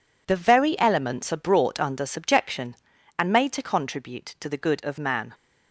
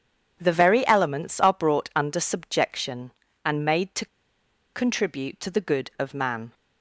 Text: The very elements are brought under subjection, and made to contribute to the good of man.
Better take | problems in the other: first | pauses between "to" and "contribute"; noticeable; at 4.0 s; 0.68 s long

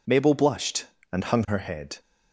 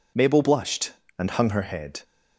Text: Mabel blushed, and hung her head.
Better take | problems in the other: neither | none

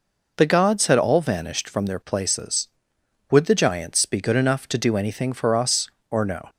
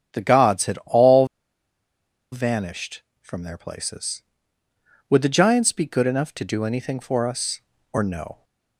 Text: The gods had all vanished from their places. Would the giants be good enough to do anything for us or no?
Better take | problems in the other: first | starts louder than the rest; strong; until 1.2 s; 8.5 dB // pauses between "all" and "vanished"; at 1.2 s; 1.0 s long

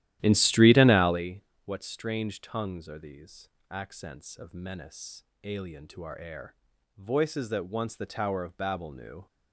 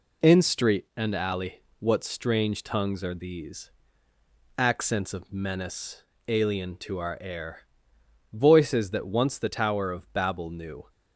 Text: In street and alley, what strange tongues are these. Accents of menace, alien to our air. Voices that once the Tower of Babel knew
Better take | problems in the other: second | starts louder than the rest; strong; until 1.3 s; 13.5 dB

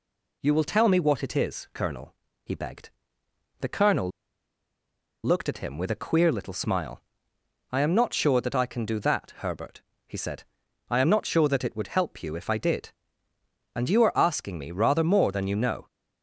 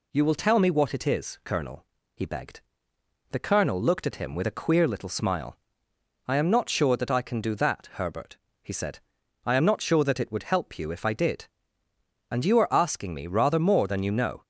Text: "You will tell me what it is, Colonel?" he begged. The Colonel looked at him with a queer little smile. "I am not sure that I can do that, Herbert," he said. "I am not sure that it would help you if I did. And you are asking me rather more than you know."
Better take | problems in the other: second | pauses between "Colonel" and "looked"; at 4.1 s; 1.1 s long

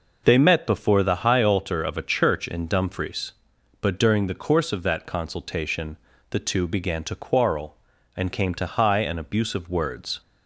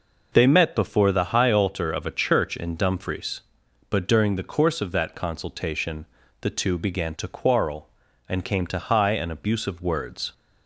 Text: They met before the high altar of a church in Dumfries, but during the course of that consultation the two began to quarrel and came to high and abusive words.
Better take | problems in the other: neither | pauses between "consultation" and "the"; slight; the same in both

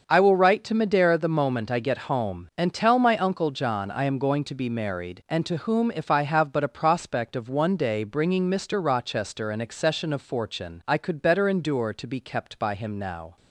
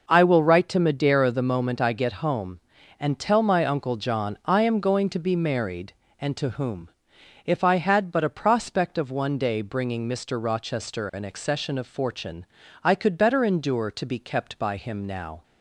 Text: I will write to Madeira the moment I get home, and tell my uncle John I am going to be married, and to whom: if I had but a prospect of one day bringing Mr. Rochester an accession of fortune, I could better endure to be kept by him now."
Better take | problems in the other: second | starts louder than the rest; until 1.0 s; 6.5 dB // says "have" for "had"; at 6.2 s

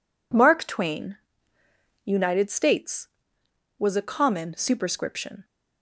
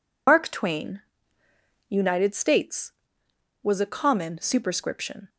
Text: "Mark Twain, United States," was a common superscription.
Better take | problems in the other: first | loses the start of "Mark"; at 0.2 s; 120 ms

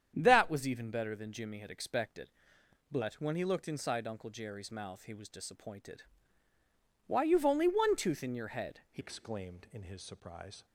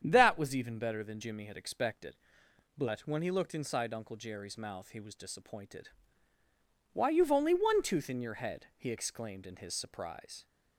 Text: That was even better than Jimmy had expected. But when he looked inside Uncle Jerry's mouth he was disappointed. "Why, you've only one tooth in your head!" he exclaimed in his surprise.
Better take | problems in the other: second | starts louder than the rest; strong; until 1.1 s; 8.5 dB; strong in the second // changes voice at "exclaimed"; from 8.9 s on; 1.7 s long

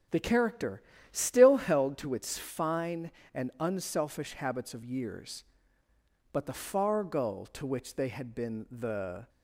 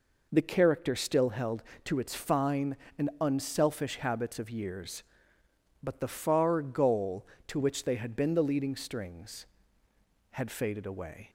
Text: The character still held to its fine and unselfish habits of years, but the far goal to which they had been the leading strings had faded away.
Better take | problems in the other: second | pauses between "character" and "still"; slight; at 0.8 s; 0.30 s long // stops before "leading strings had faded away"; at 9.2 s

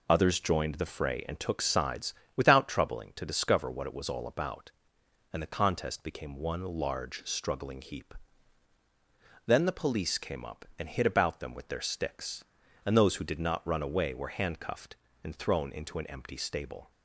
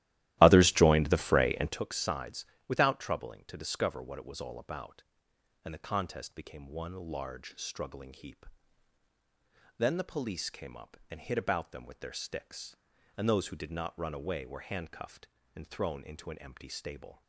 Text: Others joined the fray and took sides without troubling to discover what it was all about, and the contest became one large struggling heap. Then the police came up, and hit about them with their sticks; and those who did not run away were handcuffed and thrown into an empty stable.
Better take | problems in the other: first | starts louder than the rest; strong; until 1.8 s; 15 dB // pauses between "sides" and "without"; slight; at 2.4 s; 0.22 s long; slight in the first

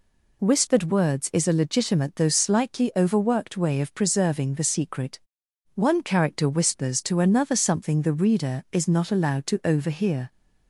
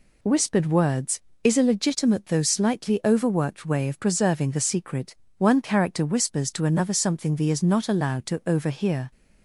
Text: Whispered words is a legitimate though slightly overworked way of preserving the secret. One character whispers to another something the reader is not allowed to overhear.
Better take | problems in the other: first | skips "reader"; at 7.4 s

